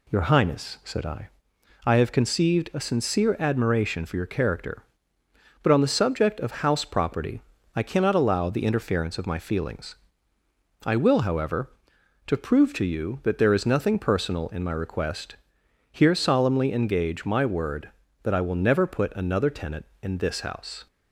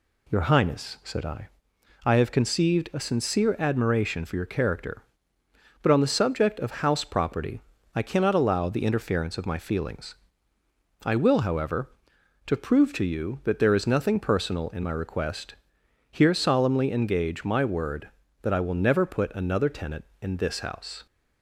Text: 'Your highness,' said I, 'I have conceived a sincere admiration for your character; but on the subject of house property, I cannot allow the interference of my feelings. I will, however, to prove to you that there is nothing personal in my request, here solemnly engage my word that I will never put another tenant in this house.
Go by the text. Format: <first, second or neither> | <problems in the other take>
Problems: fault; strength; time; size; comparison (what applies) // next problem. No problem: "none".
neither | none